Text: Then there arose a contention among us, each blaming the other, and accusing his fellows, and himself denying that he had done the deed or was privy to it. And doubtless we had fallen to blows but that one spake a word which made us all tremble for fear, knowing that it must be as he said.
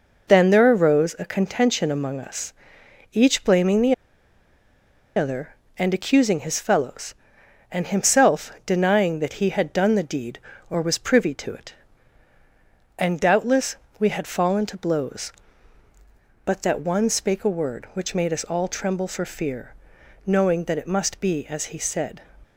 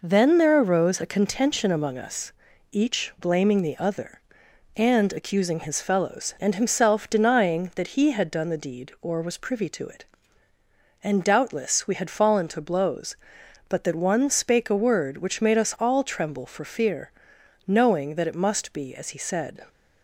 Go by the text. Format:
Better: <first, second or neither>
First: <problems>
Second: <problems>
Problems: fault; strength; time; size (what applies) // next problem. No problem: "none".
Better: second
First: pauses between "the" and "other"; at 3.9 s; 1.2 s long // pauses between "doubtless" and "we"; slight; at 13.7 s; 0.22 s long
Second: none